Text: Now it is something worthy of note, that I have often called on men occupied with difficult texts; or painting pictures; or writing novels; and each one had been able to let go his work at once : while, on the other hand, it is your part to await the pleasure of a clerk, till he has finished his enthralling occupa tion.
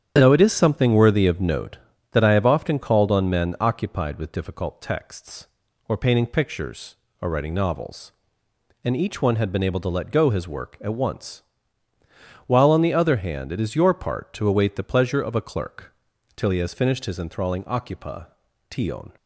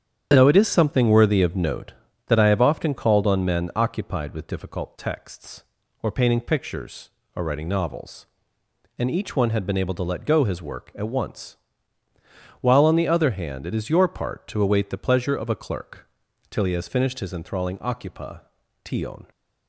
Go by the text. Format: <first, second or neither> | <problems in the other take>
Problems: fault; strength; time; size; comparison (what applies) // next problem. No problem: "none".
neither | starts louder than the rest; strong; the same in both // pauses between "occupa" and "tion"; the same in both